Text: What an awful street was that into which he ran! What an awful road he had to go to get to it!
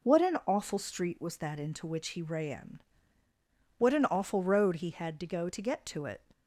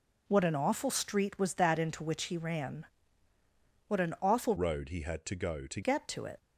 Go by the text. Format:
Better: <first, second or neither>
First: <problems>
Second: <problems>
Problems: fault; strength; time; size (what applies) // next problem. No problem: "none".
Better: first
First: none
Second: changes voice from "road" to "to"; from 4.5 to 5.8 s; 1.3 s long